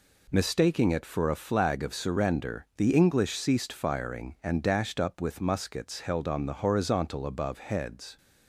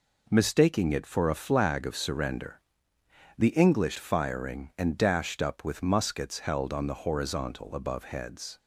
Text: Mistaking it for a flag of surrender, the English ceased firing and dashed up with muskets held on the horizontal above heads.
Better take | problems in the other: first | skips "ceased"; at 3.9 s

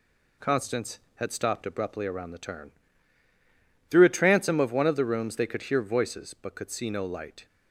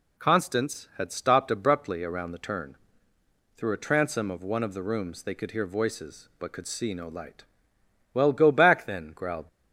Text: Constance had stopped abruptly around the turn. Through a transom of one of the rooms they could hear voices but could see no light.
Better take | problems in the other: first | goes on to say "Well go back then growled"; noticeable; from 8.1 s on; 1.3 s long

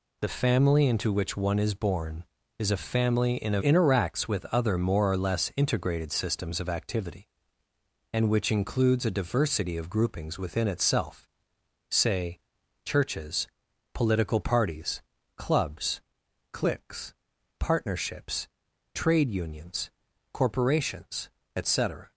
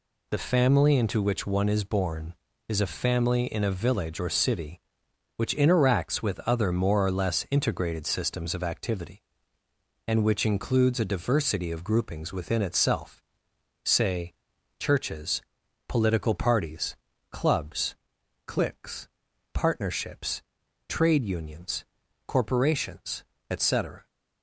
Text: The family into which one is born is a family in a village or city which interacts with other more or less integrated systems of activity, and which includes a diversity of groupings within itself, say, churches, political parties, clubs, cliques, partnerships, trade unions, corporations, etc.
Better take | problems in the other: second | skips "village or city which"; at 3.6 s

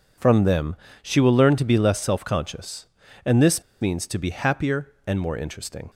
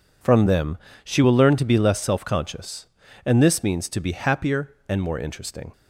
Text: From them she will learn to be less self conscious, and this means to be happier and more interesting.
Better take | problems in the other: second | pauses between "them" and "she"; slight; at 0.7 s; 0.26 s long; slight in the second // pauses between "this" and "means"; slight; at 3.6 s; 0.18 s long

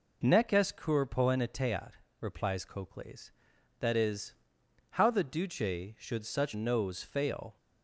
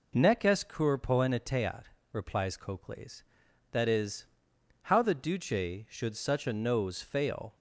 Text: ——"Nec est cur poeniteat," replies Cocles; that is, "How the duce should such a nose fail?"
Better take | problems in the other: second | skips "a"; at 6.5 s

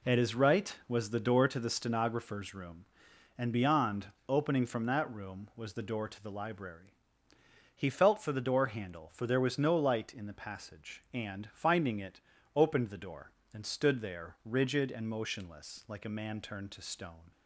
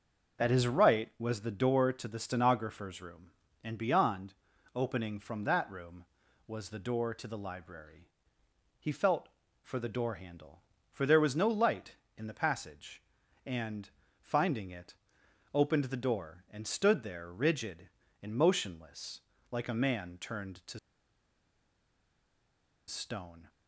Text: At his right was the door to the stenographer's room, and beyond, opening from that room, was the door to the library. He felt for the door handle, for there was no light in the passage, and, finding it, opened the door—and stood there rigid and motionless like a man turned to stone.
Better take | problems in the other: first | starts louder than the rest; until 1.4 s; 6 dB // pauses between "motionless" and "like"; slight; at 19.1 s; 0.32 s long // pauses between "to" and "stone"; strong; at 20.7 s; 2.0 s long

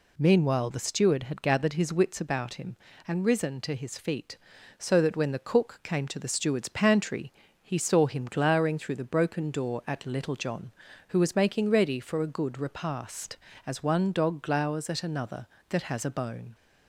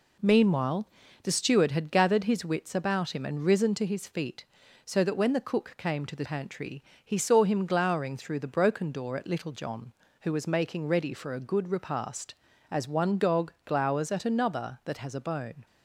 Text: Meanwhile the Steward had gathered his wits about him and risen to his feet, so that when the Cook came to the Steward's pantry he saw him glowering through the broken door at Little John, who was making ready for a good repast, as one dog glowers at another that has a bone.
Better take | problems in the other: first | pauses between "Meanwhile" and "the"; slight; at 0.8 s; 0.34 s long // skips "Steward's"; at 6.2 s // pauses between "pantry" and "he"; slight; at 6.8 s; 0.22 s long; slight in the first

